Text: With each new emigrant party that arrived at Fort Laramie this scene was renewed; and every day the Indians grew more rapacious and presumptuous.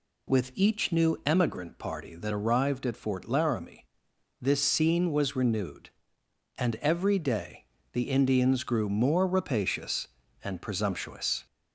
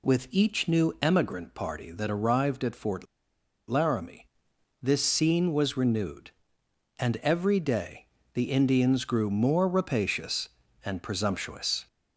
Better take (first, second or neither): first